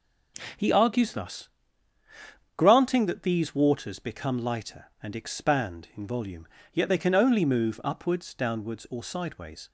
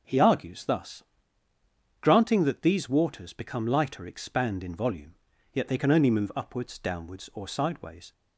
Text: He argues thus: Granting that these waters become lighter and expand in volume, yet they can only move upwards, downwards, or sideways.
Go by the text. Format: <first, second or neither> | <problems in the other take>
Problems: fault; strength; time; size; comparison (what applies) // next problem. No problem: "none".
first | skips "and"; at 4.0 s